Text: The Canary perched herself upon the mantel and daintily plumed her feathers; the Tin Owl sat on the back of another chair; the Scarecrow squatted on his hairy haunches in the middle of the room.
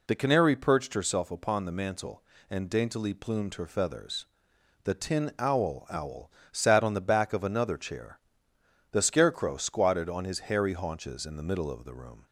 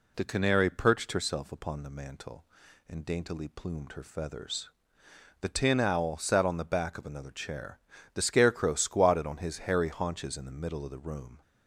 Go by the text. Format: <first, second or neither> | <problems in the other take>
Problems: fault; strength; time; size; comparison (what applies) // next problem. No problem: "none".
second | says "Owl" twice; at 5.8 s